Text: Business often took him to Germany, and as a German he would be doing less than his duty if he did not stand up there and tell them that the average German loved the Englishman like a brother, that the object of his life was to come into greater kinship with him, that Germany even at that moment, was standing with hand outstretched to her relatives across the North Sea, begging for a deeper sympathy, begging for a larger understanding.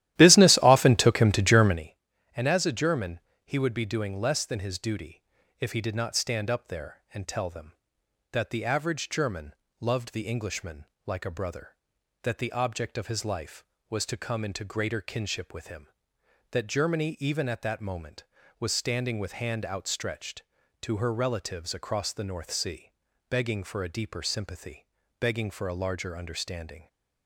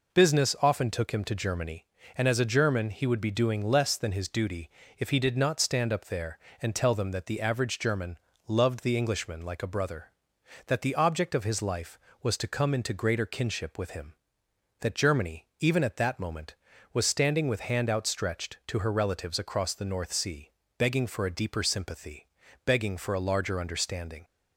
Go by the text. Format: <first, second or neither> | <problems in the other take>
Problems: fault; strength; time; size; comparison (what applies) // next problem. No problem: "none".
second | starts louder than the rest; strong; until 1.9 s; 14 dB // pauses between "German" and "he"; slight; at 3.1 s; 0.24 s long // pauses between "duty" and "if"; at 5.2 s; 0.38 s long; slight in the second // pauses between "German" and "loved"; slight; at 9.5 s; 0.28 s long; slight in the second // pauses between "Englishman" and "like"; slight; at 10.8 s; 0.20 s long